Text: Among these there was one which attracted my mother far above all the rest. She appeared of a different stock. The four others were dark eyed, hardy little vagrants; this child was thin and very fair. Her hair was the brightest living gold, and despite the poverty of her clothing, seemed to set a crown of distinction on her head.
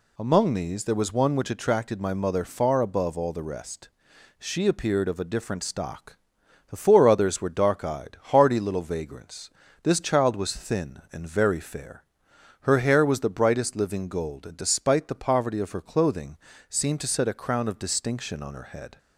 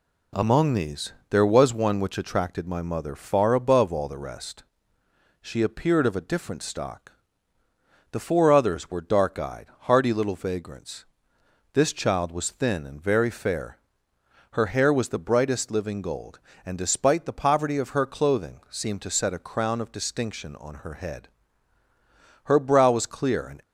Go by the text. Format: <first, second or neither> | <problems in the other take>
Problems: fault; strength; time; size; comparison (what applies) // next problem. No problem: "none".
first | pauses between "these" and "there"; slight; at 1.1 s; 0.18 s long // goes on to say "Her brow was clear and"; noticeable; from 22.4 s on; 1.1 s long